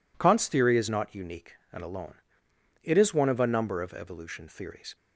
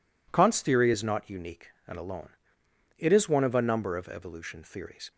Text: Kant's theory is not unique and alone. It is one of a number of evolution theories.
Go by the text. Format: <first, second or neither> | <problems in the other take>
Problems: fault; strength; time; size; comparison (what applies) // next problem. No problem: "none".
neither | none